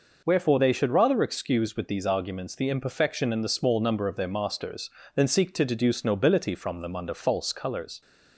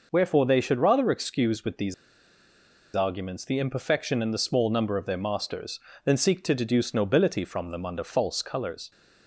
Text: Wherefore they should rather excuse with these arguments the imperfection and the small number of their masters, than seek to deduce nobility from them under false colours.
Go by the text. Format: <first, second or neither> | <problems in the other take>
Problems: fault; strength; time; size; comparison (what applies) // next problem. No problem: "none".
first | pauses between "these" and "arguments"; at 1.9 s; 1.0 s long